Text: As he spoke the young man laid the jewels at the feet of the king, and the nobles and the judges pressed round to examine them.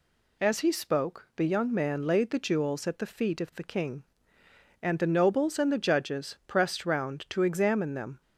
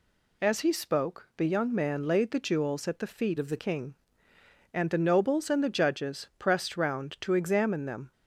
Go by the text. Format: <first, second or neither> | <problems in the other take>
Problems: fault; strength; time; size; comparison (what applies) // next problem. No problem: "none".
first | changes voice from "of" to "the"; from 3.3 to 3.5 s; 0.2 s long